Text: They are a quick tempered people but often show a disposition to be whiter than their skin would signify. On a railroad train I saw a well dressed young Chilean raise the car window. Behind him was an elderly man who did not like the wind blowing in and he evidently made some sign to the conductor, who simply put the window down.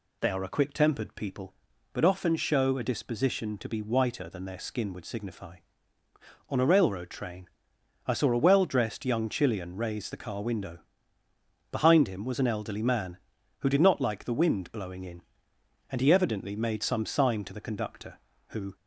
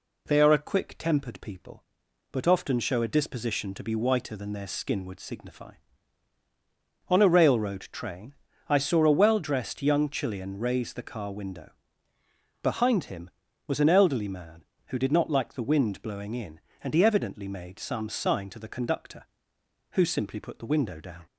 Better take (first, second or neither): second